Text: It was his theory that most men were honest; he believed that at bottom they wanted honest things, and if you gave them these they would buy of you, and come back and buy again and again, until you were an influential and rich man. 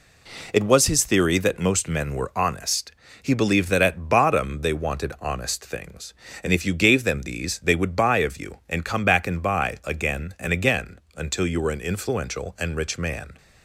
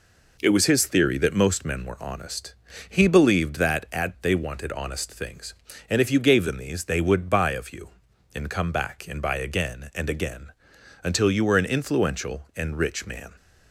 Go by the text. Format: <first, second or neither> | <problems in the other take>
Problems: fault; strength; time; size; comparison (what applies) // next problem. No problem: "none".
first | skips "bottom"; at 4.1 s